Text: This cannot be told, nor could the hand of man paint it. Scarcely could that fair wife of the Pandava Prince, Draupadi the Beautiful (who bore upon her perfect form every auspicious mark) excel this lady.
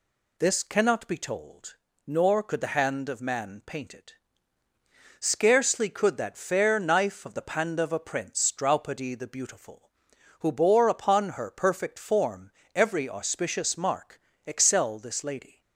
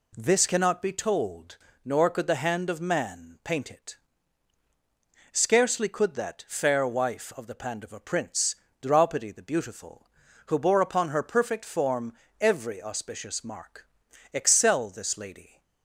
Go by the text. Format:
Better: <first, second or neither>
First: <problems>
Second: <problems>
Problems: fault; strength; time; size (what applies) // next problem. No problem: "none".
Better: second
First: says "knife" for "wife"; at 6.7 s // pauses between "form" and "every"; slight; at 12.5 s; 0.24 s long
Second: pauses between "form" and "every"; slight; at 12.1 s; 0.26 s long